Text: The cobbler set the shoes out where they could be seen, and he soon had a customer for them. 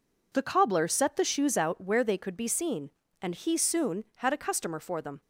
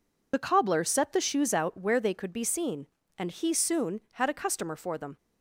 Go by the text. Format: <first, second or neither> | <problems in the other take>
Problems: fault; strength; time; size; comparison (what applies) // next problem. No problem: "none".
first | loses the start of "The"; at 0.3 s; 45 ms